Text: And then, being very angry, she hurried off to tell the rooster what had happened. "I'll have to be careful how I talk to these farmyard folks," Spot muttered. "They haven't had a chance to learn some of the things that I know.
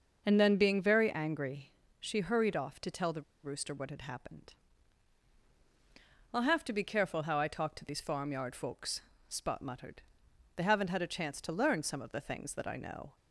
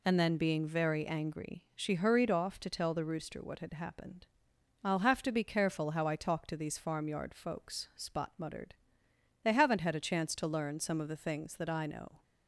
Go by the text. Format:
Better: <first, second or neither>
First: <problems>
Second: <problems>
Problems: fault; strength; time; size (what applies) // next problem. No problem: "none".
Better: second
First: starts louder than the rest; until 1.2 s; 6 dB // pauses between "the" and "rooster"; slight; at 3.2 s; 0.21 s long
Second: none